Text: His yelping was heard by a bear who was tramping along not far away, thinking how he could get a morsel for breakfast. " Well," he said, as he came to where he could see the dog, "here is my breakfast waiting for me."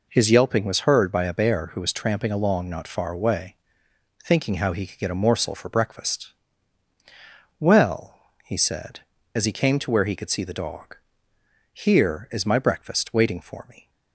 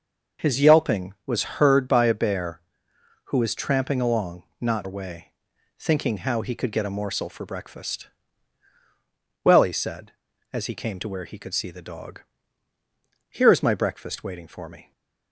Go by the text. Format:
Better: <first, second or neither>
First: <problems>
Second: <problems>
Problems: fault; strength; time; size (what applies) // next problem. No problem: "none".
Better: first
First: none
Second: starts louder than the rest; noticeable; until 1.5 s; 6 dB // skips "far"; at 4.8 s